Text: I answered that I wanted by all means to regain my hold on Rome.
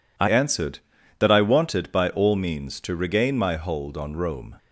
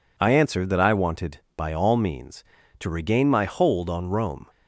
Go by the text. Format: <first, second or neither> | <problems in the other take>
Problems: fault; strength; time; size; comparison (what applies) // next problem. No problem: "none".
second | changes voice at "answered"; from 0.2 s on; 4.3 s long